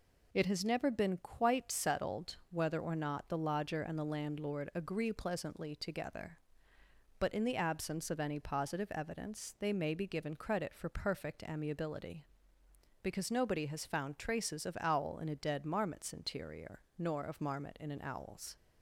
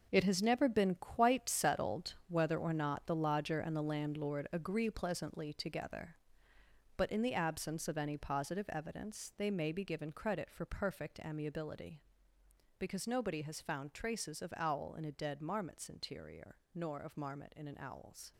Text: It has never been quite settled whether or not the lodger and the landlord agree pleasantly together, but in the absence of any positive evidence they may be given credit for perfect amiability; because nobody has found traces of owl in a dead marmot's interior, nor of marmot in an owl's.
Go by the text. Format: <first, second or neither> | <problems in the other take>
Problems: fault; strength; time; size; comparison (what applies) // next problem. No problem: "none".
first | gets quieter; strong; throughout; 10.5 dB